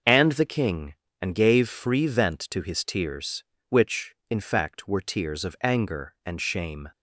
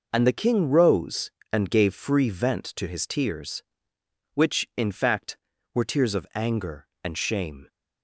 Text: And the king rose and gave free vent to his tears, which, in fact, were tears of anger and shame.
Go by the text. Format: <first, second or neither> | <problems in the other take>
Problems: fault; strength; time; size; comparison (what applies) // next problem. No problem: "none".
second | skips "rose"; at 1.0 s